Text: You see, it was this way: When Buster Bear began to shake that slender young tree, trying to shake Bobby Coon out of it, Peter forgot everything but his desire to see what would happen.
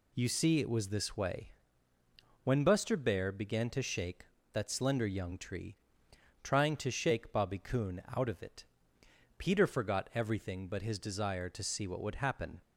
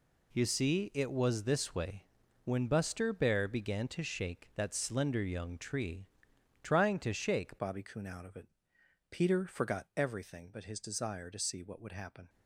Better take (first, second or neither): first